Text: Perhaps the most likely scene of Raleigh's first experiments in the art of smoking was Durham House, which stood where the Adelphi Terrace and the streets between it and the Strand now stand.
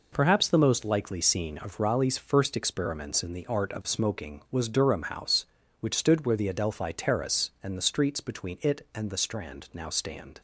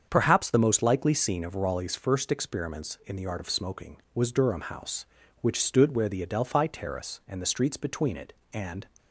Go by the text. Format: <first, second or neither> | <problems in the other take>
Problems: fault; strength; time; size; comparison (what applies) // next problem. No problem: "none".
first | starts louder than the rest; strong; until 1.1 s; 7.5 dB // stops before "the Strand now stand"; at 8.9 s